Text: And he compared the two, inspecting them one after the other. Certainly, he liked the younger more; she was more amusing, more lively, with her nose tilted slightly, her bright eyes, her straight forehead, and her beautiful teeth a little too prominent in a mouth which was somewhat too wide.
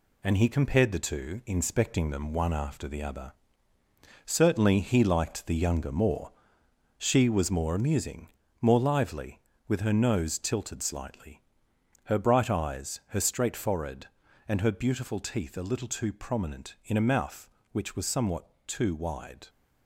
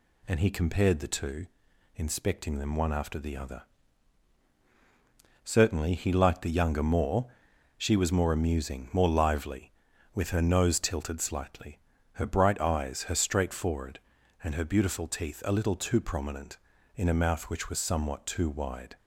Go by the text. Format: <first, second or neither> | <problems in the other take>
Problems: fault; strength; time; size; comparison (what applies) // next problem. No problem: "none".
second | gets quieter; noticeable; throughout; 5 dB // pauses between "somewhat" and "too"; slight; at 18.4 s; 0.18 s long